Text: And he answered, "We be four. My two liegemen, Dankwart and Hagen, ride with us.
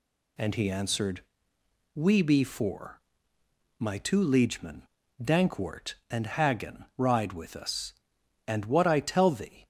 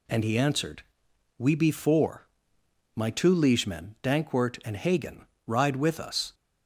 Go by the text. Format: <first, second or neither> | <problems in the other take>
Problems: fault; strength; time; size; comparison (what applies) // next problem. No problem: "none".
second | goes on to say "And what I tell thee"; noticeable; from 8.4 s on; 1.2 s long